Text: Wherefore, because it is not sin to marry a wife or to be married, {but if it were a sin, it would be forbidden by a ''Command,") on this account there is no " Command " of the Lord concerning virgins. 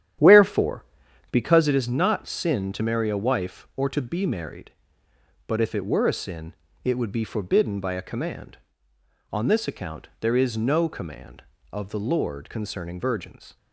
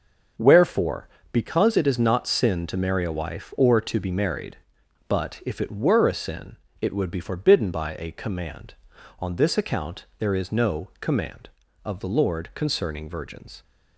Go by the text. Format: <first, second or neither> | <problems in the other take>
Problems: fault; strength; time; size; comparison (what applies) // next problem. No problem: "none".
second | starts louder than the rest; strong; until 1.8 s; 10.5 dB